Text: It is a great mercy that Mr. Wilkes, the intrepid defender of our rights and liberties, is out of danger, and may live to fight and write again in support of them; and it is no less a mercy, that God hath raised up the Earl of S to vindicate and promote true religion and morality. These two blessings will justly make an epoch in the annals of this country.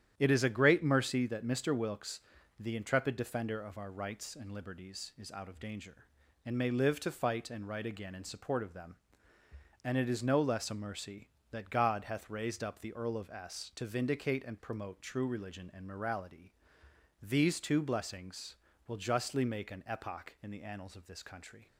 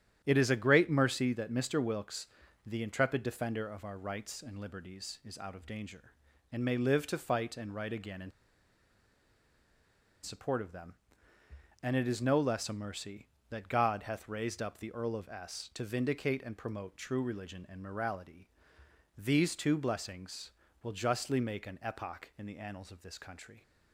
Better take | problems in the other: first | starts louder than the rest; strong; until 1.2 s; 10.5 dB; strong in the first // pauses between "in" and "support"; strong; at 8.3 s; 1.9 s long

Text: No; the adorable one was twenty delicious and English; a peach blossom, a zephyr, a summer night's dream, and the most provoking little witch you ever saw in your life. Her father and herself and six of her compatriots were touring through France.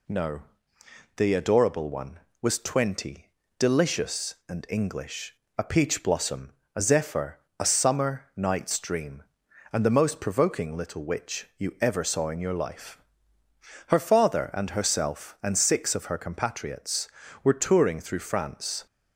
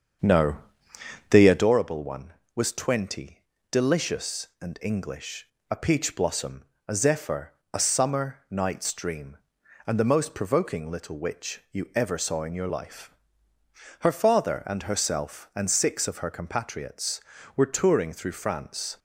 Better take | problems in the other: first | starts louder than the rest; strong; until 1.7 s; 7.5 dB // pauses between "twenty" and "delicious"; slight; at 3.4 s; 0.28 s long; slight in the first

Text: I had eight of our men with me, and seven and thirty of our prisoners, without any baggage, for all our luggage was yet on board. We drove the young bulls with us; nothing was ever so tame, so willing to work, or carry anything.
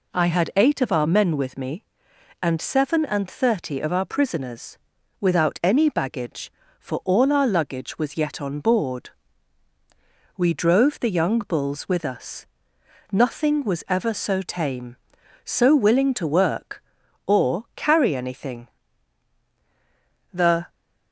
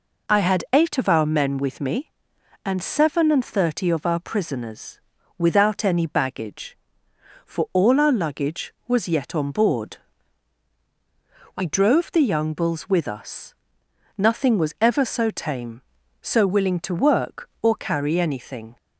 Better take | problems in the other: second | goes on to say "The"; slight; from 20.3 s on; 0.36 s long

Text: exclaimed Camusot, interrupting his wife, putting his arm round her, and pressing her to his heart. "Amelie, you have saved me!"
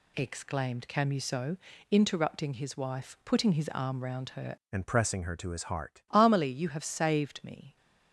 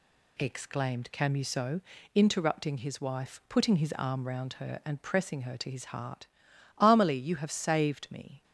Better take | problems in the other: second | changes voice from "and" to "heart"; from 4.7 to 6.0 s; 1.3 s long

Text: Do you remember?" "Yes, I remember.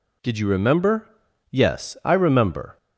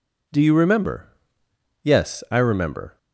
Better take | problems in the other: second | says "Did" for "Do"; at 0.2 s

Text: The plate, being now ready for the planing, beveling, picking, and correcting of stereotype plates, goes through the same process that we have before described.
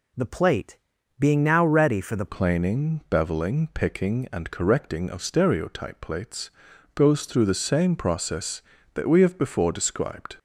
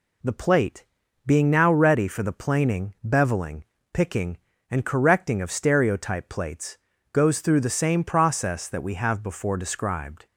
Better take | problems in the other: second | changes voice at "planing"; from 2.2 s on; 8.1 s long

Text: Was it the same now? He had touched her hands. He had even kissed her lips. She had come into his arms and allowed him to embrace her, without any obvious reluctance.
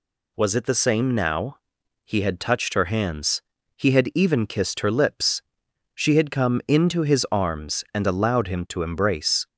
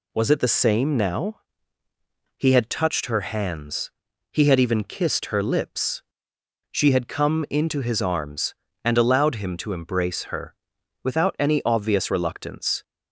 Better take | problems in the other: second | stops before "her without any obvious reluctance"; at 9.4 s

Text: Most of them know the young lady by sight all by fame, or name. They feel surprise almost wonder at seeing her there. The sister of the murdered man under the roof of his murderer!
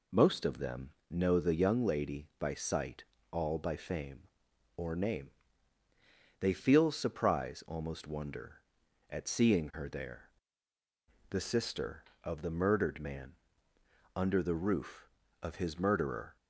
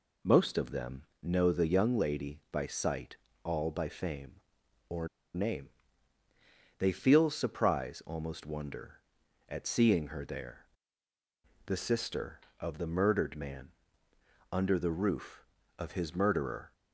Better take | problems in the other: first | pauses between "them" and "know"; slight; at 1.0 s; 0.20 s long; slight in the first // pauses between "sight" and "all"; slight; at 3.1 s; 0.26 s long; slight in the first // pauses between "or" and "name"; slight; at 5.0 s; 0.28 s long // pauses between "man" and "under"; noticeable; at 13.6 s; 0.84 s long; noticeable in the first

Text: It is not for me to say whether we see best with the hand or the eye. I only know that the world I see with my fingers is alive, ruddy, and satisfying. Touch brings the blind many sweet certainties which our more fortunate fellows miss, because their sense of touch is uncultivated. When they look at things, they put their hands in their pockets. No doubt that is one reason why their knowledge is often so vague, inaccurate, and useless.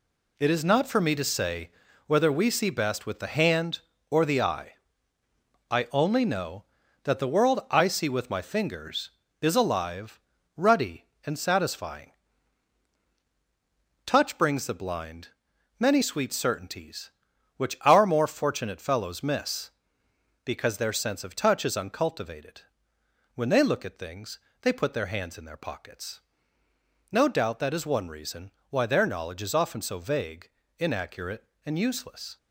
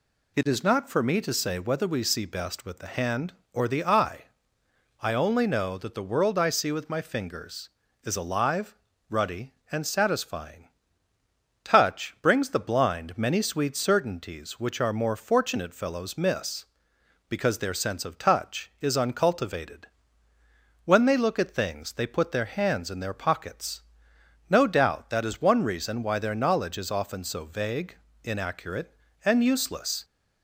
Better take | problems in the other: second | gets quieter; strong; throughout; 8 dB // pauses between "say" and "whether"; at 1.6 s; 0.38 s long // pauses between "blind" and "many"; noticeable; at 15.2 s; 0.48 s long // pauses between "reason" and "why"; slight; at 28.5 s; 0.18 s long

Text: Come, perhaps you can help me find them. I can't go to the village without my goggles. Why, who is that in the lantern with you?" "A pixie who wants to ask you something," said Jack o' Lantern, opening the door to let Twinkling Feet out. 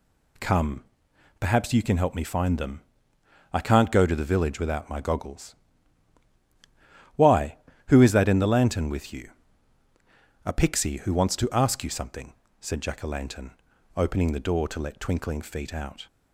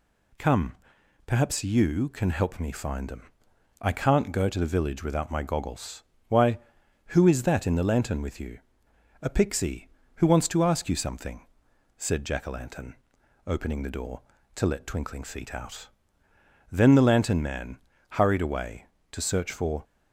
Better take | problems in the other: first | goes on to say "Then the lantern man hurried away to search for"; strong; from 16.7 s on; 3.1 s long

